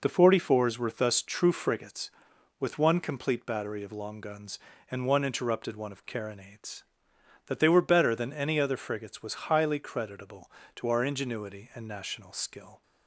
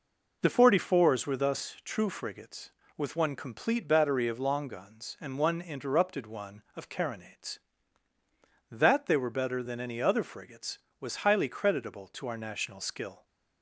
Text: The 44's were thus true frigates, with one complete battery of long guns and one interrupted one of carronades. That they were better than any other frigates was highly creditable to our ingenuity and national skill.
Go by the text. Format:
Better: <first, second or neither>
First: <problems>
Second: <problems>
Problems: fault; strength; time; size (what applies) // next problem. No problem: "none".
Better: first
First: none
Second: skips "ingenuity and"; at 12.3 s